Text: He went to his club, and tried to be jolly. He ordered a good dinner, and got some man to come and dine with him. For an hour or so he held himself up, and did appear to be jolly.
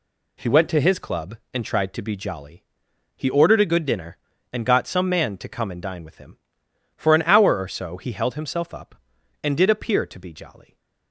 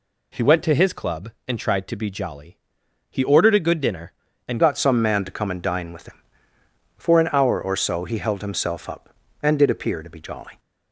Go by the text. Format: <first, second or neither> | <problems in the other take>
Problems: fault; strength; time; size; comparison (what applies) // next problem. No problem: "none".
first | changes voice at "got"; from 4.5 s on; 6.0 s long